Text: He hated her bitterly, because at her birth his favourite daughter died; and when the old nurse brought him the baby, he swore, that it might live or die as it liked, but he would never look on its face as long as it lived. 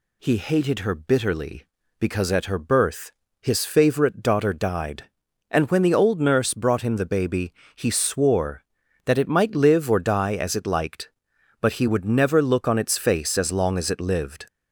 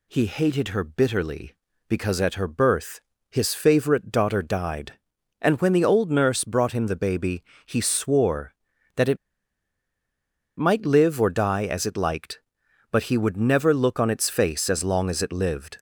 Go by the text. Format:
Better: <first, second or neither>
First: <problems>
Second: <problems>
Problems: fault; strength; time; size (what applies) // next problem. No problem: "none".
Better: first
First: pauses between "birth" and "his"; slight; at 3.1 s; 0.28 s long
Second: pauses between "birth" and "his"; slight; at 3.0 s; 0.28 s long // pauses between "it" and "might"; strong; at 9.1 s; 1.4 s long